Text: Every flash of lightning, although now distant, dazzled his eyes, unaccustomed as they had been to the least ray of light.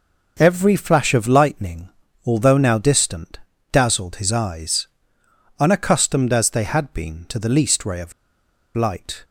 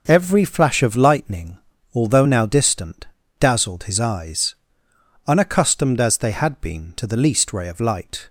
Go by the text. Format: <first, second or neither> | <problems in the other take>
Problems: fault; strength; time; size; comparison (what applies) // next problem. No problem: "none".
second | pauses between "of" and "light"; noticeable; at 8.1 s; 0.63 s long